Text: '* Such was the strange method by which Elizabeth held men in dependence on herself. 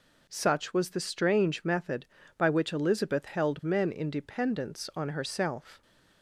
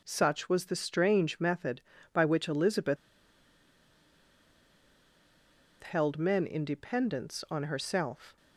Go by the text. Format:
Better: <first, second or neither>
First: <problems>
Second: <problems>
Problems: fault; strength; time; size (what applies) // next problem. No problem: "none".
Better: first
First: none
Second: pauses between "Elizabeth" and "held"; strong; at 2.9 s; 2.8 s long